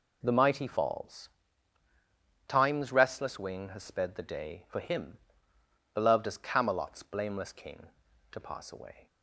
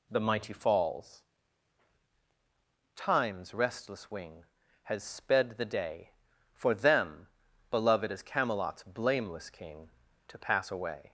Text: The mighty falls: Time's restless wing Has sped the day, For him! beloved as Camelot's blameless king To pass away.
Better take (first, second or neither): first